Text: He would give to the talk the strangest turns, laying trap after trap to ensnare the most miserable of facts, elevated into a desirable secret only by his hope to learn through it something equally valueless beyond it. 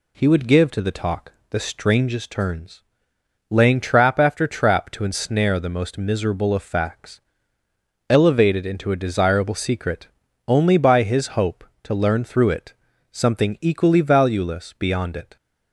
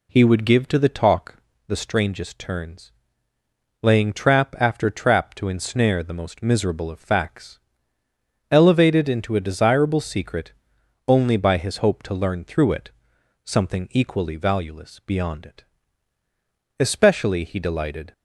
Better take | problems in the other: first | pauses between "talk" and "the"; slight; at 1.3 s; 0.32 s long; slight in the first // pauses between "secret" and "only"; noticeable; at 10.5 s; 0.56 s long; also in the first // pauses between "it" and "something"; noticeable; at 12.9 s; 0.54 s long; also in the first // goes on to say "Especially he delighted"; from 16.8 s on; 1.3 s long

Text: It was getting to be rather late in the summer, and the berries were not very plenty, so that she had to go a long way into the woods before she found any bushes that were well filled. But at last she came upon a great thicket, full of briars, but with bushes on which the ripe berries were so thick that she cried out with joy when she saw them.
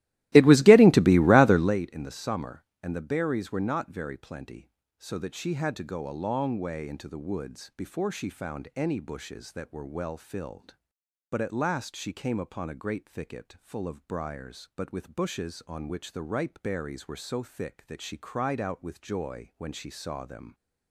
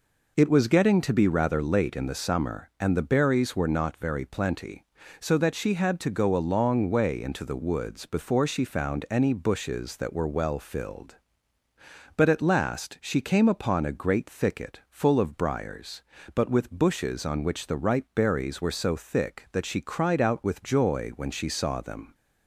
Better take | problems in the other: second | starts louder than the rest; strong; until 1.8 s; 17 dB

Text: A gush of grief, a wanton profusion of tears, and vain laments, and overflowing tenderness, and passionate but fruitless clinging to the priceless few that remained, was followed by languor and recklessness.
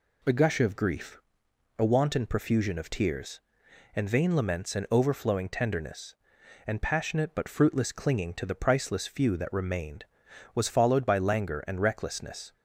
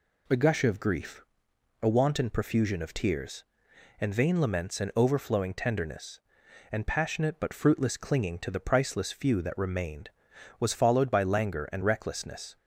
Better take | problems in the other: neither | none

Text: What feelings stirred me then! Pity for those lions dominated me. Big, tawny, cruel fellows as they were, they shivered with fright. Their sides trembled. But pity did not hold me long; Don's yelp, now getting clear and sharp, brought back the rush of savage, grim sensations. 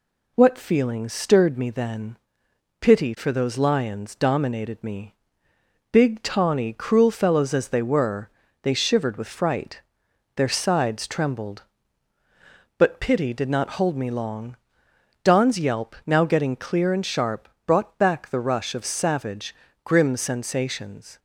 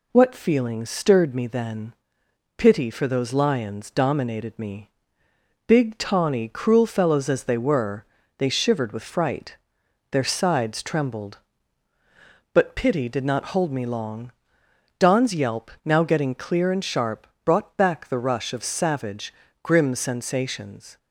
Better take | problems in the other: neither | none

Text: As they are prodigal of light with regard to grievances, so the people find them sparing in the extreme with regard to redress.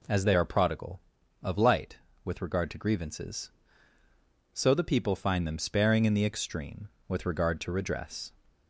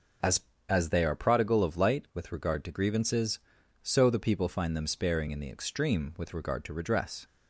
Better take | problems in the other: first | starts louder than the rest; until 1.5 s; 6.5 dB // says "As" twice; at 0.6 s

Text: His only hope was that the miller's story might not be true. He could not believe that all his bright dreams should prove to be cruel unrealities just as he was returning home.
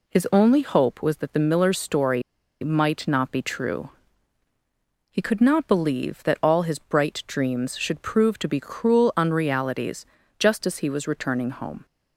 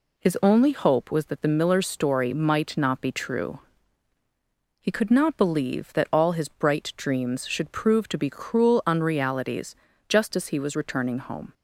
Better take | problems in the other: second | pauses between "story" and "might"; at 2.2 s; 0.41 s long // pauses between "unrealities" and "just"; slight; at 10.0 s; 0.34 s long; slight in the second

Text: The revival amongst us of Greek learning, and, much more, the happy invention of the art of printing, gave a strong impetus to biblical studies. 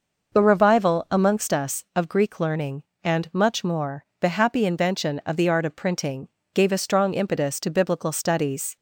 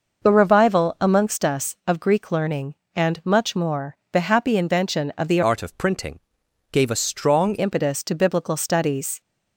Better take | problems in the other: first | changes voice from "art" to "strong"; from 5.4 to 7.5 s; 2.1 s long

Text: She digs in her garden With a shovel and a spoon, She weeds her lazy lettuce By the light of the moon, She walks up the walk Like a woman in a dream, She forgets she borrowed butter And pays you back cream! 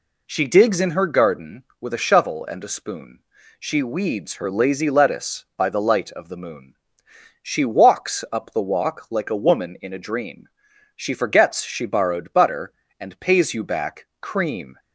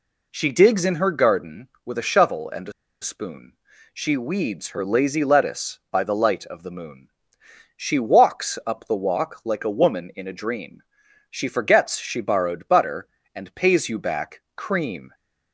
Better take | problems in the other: first | pauses between "a" and "spoon"; slight; at 2.7 s; 0.29 s long

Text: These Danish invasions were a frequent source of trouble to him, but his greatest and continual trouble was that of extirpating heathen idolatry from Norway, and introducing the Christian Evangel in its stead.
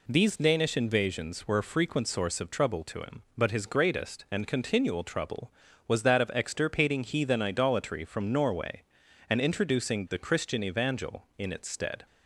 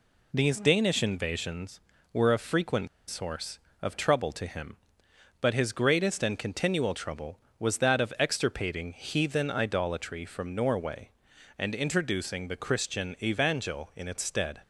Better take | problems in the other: first | pauses between "frequent" and "source"; slight; at 2.8 s; 0.20 s long

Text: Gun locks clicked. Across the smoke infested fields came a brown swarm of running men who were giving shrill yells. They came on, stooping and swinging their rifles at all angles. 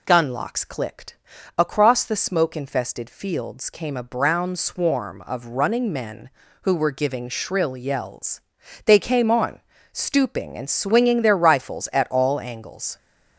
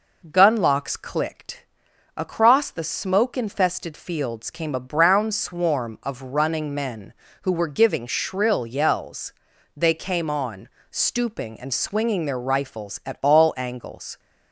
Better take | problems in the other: first | starts louder than the rest; noticeable; until 1.8 s; 5 dB

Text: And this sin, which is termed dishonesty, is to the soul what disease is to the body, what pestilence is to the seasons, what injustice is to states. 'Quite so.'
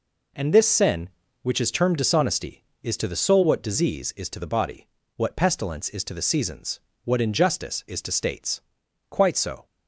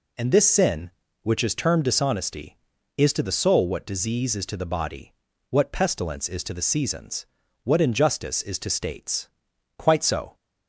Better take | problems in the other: neither | none

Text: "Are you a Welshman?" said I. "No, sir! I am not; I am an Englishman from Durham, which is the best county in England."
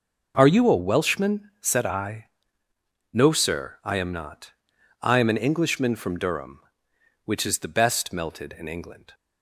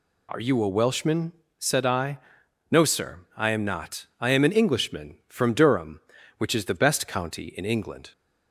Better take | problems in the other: second | says "melted" for "county"; at 8.1 s

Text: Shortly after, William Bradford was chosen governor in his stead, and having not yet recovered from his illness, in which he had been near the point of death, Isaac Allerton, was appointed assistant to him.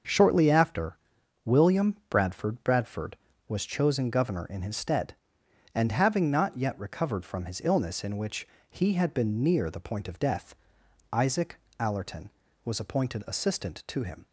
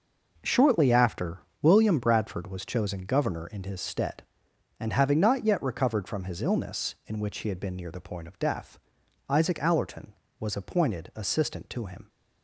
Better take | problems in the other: second | starts louder than the rest; until 1.5 s; 6.5 dB // says "Bradford" twice; at 2.6 s // pauses between "which" and "he"; slight; at 8.4 s; 0.24 s long // pauses between "Isaac" and "Allerton"; slight; at 11.5 s; 0.22 s long

